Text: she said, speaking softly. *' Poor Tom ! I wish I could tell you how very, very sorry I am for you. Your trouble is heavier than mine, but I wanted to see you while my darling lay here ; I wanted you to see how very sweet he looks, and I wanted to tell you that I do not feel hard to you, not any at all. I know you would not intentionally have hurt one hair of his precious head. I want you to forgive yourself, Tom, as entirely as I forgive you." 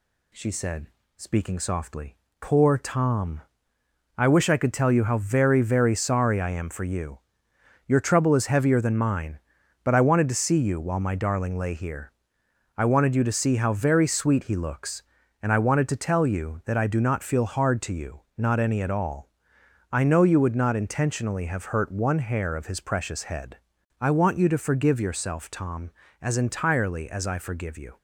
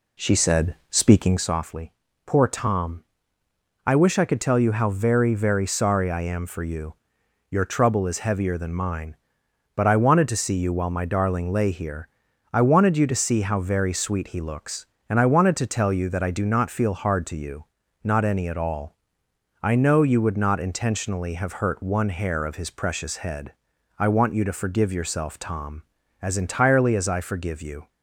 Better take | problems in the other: first | starts louder than the rest; slight; until 1.5 s; 2 dB

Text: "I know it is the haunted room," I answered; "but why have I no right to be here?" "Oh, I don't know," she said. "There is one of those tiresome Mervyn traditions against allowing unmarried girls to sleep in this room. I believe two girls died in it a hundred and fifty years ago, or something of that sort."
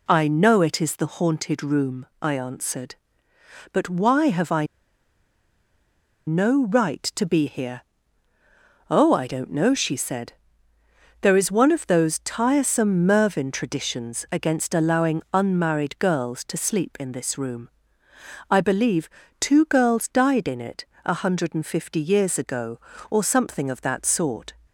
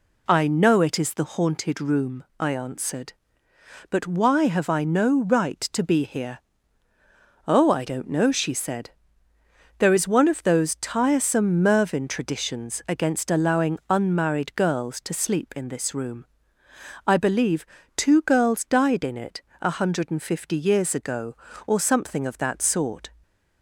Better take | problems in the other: second | pauses between "I" and "no"; strong; at 4.6 s; 1.6 s long // pauses between "believe" and "two"; slight; at 19.0 s; 0.32 s long; slight in the second // pauses between "it" and "a"; slight; at 20.8 s; 0.22 s long; slight in the second

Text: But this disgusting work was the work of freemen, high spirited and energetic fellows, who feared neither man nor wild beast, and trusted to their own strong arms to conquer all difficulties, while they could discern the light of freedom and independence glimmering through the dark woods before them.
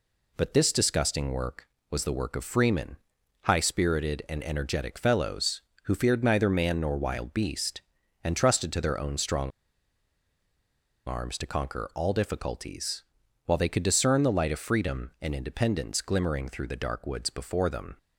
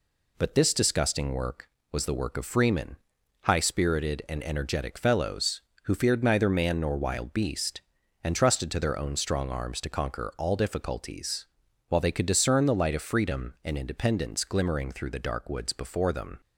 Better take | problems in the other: second | pauses between "strong" and "arms"; strong; at 9.5 s; 1.5 s long

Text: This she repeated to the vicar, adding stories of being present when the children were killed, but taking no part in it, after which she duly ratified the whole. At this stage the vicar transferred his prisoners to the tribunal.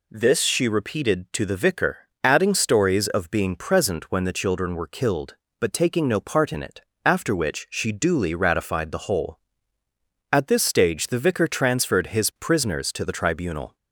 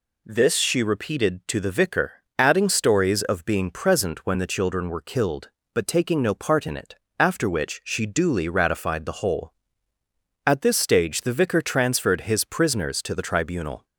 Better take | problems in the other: neither | none

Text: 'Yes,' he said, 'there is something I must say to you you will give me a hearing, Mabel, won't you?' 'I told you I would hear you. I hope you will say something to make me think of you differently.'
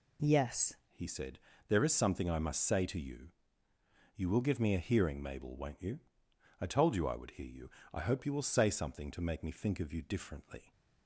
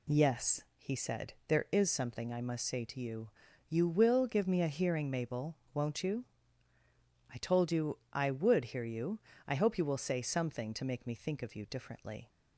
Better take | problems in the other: second | changes voice at "he"; from 0.8 s on; 9.9 s long // pauses between "you" and "you"; noticeable; at 3.2 s; 0.86 s long; also in the second

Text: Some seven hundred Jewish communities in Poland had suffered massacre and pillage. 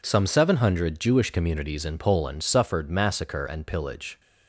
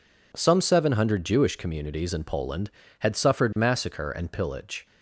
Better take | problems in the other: second | skips "had"; at 2.4 s

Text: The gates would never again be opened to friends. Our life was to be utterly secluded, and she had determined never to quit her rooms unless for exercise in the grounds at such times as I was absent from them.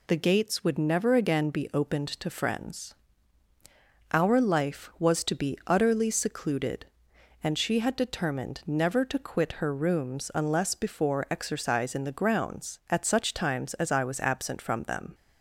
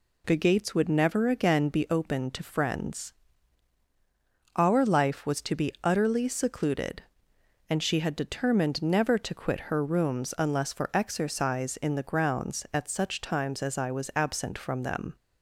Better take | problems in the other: second | says "before" for "for"; at 10.7 s

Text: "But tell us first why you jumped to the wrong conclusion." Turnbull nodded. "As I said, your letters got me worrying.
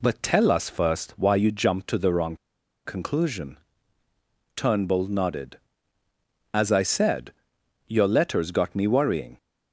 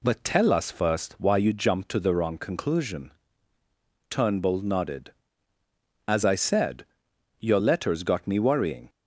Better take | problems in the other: second | pauses between "wrong" and "conclusion"; noticeable; at 2.3 s; 0.49 s long

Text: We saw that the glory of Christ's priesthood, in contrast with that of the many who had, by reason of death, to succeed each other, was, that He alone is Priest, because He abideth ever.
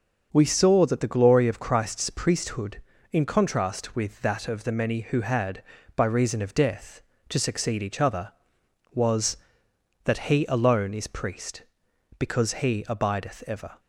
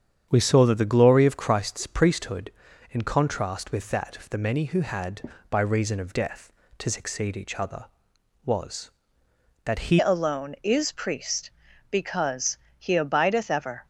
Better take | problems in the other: first | starts louder than the rest; strong; until 1.3 s; 8 dB; also in the first // changes voice at "alone"; from 9.9 s on; 3.9 s long // pauses between "because" and "He"; slight; at 12.5 s; 0.20 s long

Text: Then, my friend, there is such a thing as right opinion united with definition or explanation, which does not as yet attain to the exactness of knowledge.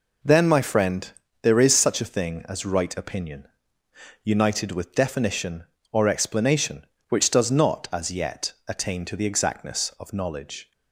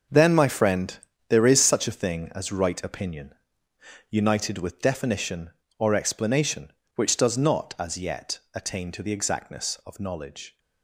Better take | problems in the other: first | gets quieter; strong; throughout; 10.5 dB // pauses between "opinion" and "united"; noticeable; at 3.3 s; 0.76 s long; noticeable in the first // pauses between "yet" and "attain"; slight; at 8.3 s; 0.16 s long; slight in the first

